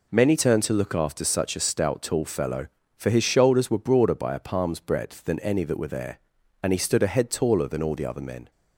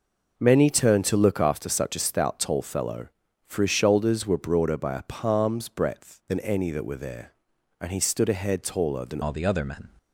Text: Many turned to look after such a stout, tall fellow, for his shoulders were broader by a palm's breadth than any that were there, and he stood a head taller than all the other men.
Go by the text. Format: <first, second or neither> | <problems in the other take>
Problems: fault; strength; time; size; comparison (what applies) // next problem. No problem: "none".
first | changes voice at "all"; from 9.2 s on; 0.6 s long